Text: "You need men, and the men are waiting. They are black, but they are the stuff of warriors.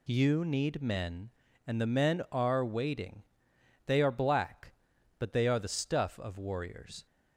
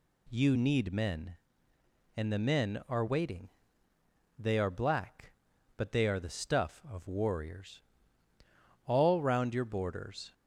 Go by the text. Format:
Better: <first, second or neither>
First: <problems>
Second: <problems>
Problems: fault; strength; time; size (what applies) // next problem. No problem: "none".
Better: first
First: none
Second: goes on to say "All round your borders"; from 8.8 s on; 1.4 s long